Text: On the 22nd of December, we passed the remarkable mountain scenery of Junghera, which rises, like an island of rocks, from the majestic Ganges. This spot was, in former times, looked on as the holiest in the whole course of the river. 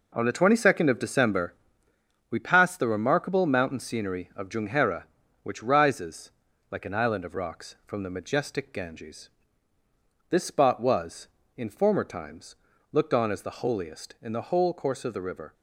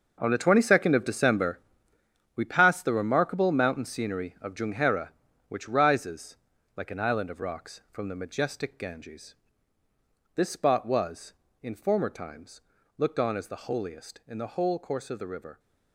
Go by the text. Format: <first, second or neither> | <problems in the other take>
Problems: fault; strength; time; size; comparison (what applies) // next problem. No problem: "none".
first | gets quieter; strong; throughout; 12 dB